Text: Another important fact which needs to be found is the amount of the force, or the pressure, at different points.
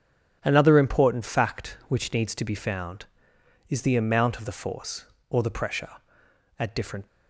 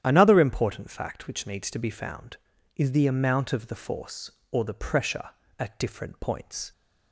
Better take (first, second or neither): second